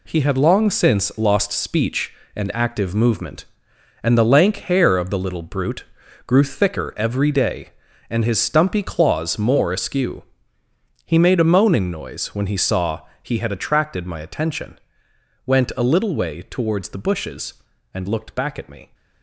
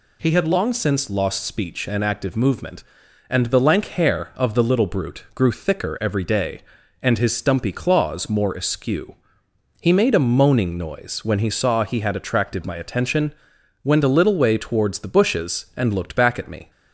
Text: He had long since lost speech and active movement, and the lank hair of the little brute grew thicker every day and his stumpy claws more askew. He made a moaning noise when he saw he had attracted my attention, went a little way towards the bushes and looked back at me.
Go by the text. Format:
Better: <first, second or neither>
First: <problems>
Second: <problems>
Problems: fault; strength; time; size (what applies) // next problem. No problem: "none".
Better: second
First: gets quieter; strong; throughout; 7.5 dB // pauses between "brute" and "grew"; at 5.8 s; 0.44 s long // pauses between "saw" and "he"; slight; at 13.0 s; 0.20 s long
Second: none